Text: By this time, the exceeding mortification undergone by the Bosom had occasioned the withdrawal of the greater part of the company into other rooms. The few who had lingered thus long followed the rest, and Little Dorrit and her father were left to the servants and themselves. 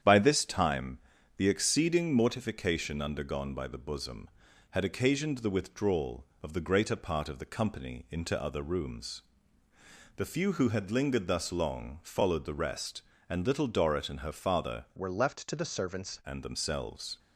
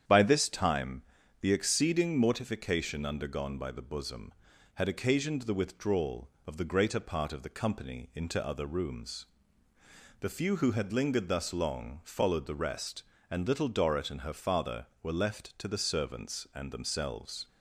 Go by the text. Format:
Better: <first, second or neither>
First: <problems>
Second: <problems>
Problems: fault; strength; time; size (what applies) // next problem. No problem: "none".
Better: second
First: starts louder than the rest; strong; until 1.4 s; 9 dB // changes voice from "were" to "servants"; from 14.9 to 16.2 s; 1.3 s long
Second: starts louder than the rest; strong; until 1.4 s; 9 dB